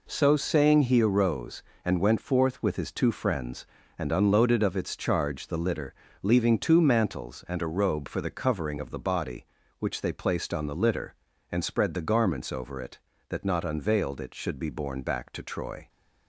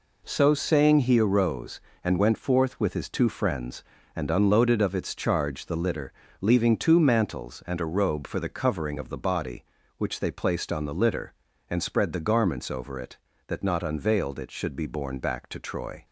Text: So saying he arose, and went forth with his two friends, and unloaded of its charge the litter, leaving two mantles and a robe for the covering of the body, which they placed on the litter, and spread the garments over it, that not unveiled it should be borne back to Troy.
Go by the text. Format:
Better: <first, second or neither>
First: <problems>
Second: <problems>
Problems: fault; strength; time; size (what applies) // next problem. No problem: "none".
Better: neither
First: none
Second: none